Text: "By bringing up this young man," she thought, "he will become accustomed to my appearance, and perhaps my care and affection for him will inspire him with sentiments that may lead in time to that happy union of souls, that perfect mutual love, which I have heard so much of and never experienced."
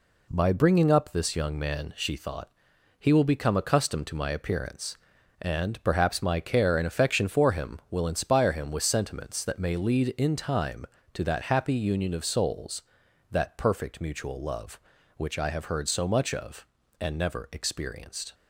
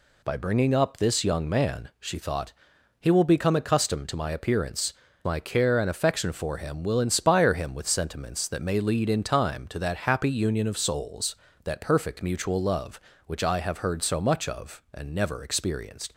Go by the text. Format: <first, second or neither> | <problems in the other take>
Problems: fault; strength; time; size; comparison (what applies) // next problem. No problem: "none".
first | skips "and perhaps"; at 5.0 s